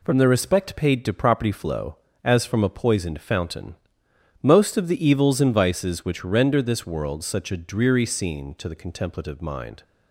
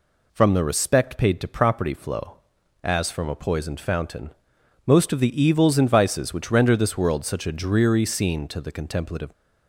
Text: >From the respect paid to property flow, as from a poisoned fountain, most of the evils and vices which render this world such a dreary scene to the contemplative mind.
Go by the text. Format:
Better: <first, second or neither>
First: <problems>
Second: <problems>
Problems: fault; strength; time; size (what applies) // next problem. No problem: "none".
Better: first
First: none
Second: stops before "mind"; at 9.3 s